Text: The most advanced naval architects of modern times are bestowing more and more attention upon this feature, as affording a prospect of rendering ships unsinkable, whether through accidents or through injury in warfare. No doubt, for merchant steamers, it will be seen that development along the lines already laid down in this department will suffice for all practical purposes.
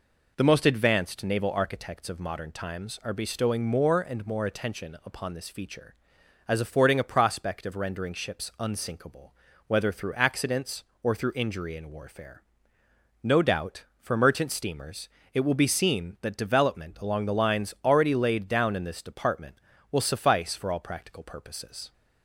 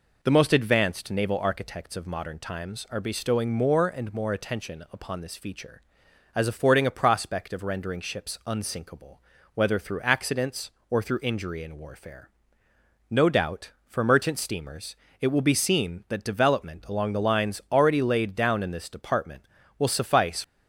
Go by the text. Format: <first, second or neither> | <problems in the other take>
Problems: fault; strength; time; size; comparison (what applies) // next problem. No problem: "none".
first | stops before "for all practical purposes"; at 20.4 s